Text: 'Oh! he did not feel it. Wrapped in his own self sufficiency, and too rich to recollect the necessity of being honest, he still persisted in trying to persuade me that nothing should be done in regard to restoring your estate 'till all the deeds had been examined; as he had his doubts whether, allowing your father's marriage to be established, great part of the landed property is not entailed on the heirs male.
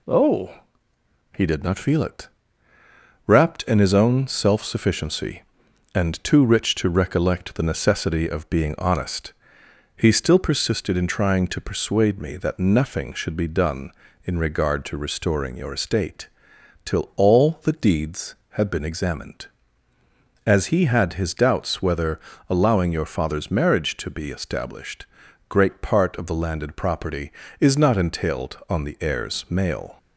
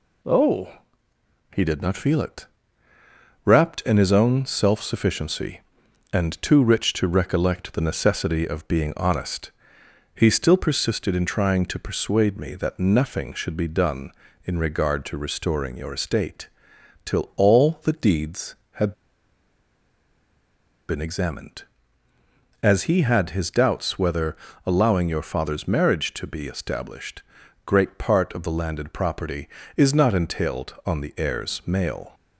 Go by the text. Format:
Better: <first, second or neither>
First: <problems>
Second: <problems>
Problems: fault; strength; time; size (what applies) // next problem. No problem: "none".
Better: first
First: pauses between "estate" and "till"; noticeable; at 16.2 s; 0.56 s long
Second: pauses between "estate" and "till"; noticeable; at 16.4 s; 0.56 s long // pauses between "had" and "been"; strong; at 18.9 s; 1.9 s long